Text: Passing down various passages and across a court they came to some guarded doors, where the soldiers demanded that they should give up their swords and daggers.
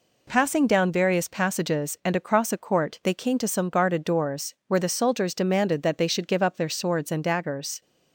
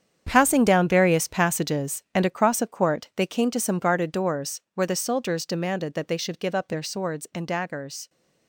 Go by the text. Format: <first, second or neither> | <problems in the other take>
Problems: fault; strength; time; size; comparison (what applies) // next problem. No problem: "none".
first | gets quieter; strong; throughout; 12.5 dB